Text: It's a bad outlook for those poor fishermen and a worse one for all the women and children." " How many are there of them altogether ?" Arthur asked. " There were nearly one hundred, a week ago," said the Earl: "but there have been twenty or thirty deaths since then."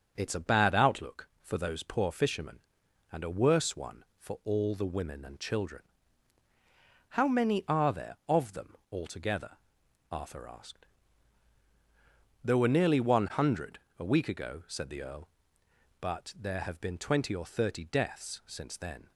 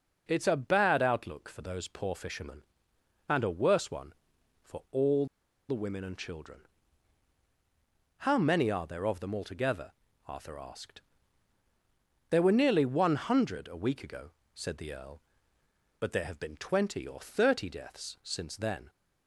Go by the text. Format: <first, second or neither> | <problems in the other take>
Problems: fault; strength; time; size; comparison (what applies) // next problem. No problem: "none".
first | starts louder than the rest; strong; until 1.2 s; 8 dB; strong in the first // pauses between "all" and "the"; at 5.2 s; 0.43 s long